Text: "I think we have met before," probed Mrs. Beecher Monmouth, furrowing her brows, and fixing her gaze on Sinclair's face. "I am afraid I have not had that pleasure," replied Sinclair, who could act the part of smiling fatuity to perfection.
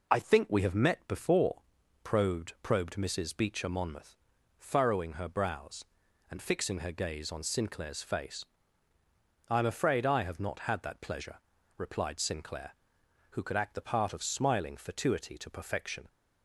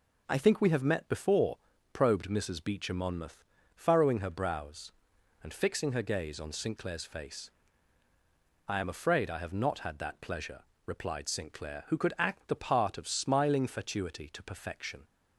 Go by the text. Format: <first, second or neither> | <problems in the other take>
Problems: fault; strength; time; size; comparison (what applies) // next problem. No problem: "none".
second | says "probed" twice; at 2.6 s